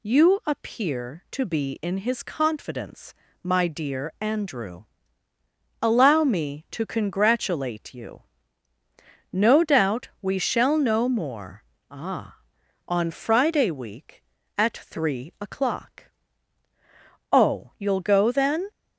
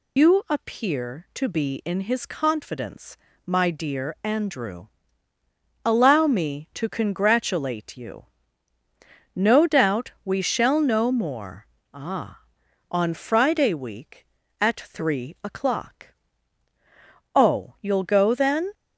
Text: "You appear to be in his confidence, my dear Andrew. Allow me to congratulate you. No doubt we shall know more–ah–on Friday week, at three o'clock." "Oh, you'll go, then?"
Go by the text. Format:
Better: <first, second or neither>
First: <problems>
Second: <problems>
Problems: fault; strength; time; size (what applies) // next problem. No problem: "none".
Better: first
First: none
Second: loses the start of "You"; at 0.1 s; 115 ms